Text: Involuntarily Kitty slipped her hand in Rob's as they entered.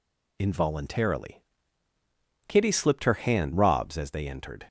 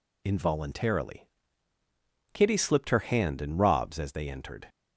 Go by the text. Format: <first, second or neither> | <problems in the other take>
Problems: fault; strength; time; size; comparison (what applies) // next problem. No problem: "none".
second | pauses between "Involuntarily" and "Kitty"; at 1.4 s; 1.0 s long; also in the second // skips "in"; at 3.5 s